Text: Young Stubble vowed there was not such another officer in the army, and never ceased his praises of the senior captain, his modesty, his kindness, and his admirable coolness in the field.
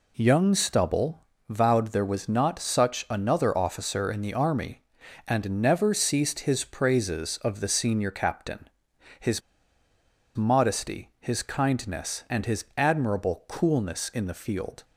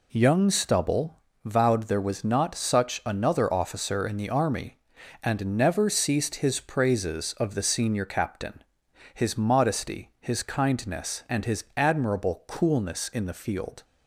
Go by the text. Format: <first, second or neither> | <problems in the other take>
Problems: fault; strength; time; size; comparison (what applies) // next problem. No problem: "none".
second | pauses between "Stubble" and "vowed"; slight; at 1.2 s; 0.22 s long; slight in the second // pauses between "his" and "modesty"; noticeable; at 9.4 s; 0.95 s long